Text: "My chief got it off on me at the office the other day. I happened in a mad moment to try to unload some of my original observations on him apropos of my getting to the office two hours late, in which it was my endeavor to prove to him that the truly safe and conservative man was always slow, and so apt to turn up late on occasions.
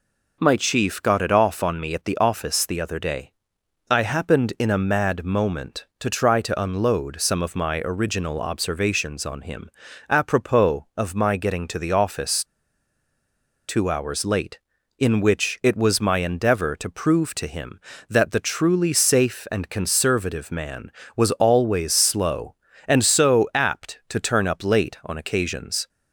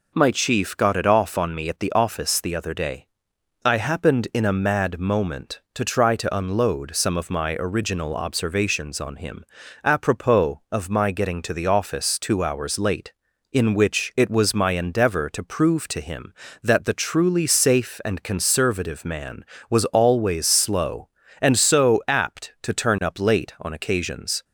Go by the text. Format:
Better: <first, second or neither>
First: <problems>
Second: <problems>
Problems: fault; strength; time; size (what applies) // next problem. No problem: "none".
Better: second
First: pauses between "him" and "apropos"; at 9.6 s; 0.40 s long // pauses between "office" and "two"; at 12.4 s; 1.2 s long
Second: pauses between "him" and "apropos"; at 9.4 s; 0.40 s long